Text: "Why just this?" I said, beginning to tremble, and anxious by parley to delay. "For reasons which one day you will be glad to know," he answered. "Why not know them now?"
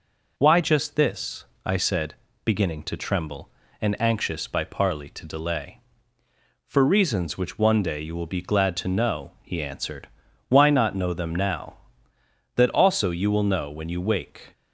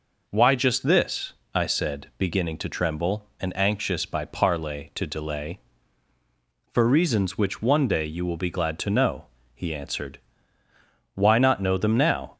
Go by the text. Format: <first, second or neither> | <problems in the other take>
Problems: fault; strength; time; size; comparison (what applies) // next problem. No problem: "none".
second | goes on to say "That also you will know when you wake"; strong; from 12.5 s on; 1.9 s long